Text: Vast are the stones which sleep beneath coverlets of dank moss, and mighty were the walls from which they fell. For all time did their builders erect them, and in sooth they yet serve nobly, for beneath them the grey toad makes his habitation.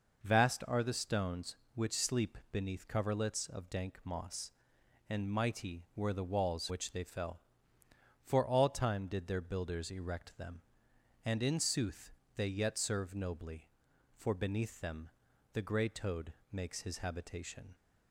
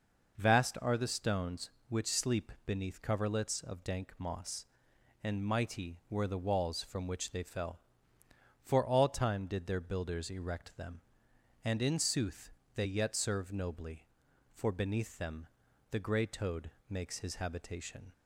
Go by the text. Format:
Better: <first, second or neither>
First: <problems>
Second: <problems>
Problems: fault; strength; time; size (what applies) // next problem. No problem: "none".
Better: second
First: pauses between "sleep" and "beneath"; slight; at 2.3 s; 0.16 s long // skips "from"; at 6.6 s // pauses between "sooth" and "they"; slight; at 12.1 s; 0.24 s long // pauses between "them" and "the"; at 15.1 s; 0.42 s long // pauses between "toad" and "makes"; slight; at 16.3 s; 0.18 s long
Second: pauses between "sleep" and "beneath"; slight; at 2.4 s; 0.16 s long // pauses between "sooth" and "they"; slight; at 12.4 s; 0.24 s long // pauses between "them" and "the"; at 15.4 s; 0.42 s long // pauses between "toad" and "makes"; slight; at 16.7 s; 0.18 s long